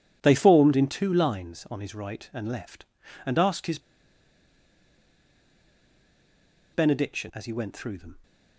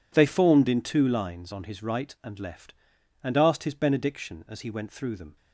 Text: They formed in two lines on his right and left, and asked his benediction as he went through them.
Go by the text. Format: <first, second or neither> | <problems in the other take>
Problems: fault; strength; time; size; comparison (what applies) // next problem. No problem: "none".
second | pauses between "his" and "benediction"; strong; at 3.7 s; 2.9 s long